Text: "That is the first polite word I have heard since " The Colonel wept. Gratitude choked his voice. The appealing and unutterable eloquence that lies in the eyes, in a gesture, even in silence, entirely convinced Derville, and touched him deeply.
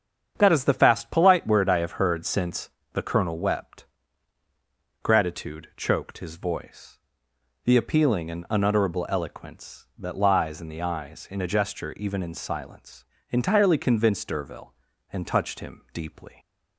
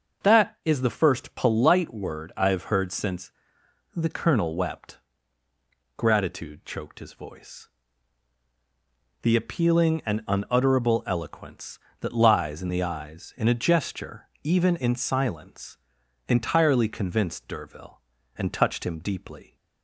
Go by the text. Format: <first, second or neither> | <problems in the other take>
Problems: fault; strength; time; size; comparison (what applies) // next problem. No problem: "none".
second | starts louder than the rest; strong; until 1.4 s; 8 dB; also in the second // says "fast" for "first"; at 0.7 s